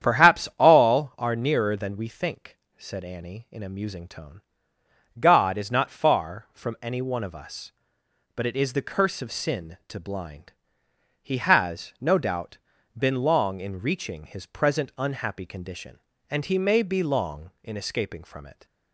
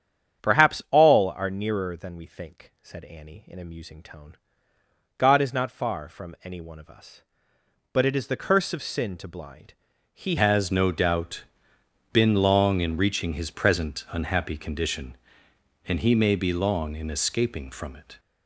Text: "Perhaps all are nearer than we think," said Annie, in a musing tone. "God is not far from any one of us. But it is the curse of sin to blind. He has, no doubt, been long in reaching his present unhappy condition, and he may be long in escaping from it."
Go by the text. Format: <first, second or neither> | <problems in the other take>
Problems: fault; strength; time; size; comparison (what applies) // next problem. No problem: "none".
first | starts louder than the rest; strong; until 1.5 s; 8.5 dB; strong in the first // changes voice at "has"; from 10.3 s on; 7.8 s long